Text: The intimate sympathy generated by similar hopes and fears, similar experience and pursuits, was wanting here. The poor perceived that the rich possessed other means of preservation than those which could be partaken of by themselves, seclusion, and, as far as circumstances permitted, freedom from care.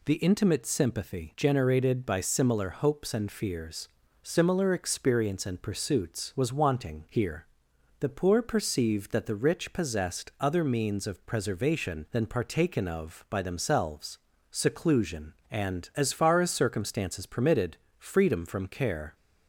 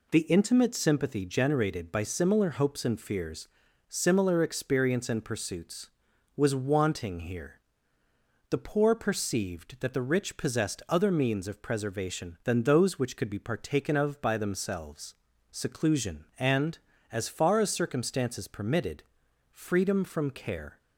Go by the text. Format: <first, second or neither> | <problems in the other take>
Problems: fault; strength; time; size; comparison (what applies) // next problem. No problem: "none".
second | skips "those which could be"; at 12.2 s